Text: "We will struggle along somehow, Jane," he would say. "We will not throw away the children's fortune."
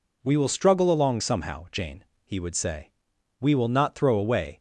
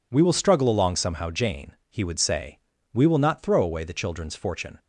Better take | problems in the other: second | stops before "the children's fortune"; at 4.5 s

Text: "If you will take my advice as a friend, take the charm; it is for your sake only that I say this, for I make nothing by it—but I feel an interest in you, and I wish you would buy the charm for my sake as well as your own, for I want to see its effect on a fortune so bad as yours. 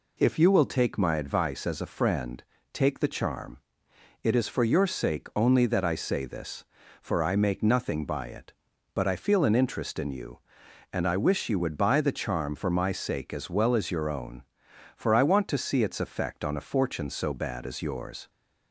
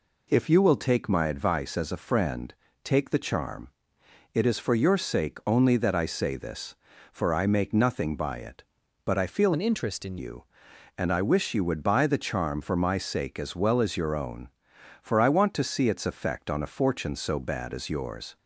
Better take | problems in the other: first | changes voice from "an" to "in"; from 9.5 to 10.1 s; 0.6 s long

